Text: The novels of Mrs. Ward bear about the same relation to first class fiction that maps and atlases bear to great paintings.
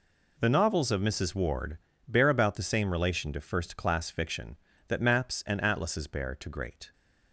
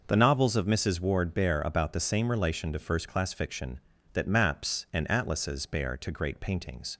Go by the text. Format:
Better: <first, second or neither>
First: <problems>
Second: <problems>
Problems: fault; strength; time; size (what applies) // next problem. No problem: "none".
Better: second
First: pauses between "Ward" and "bear"; slight; at 1.7 s; 0.28 s long // stops before "paintings"; at 6.9 s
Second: none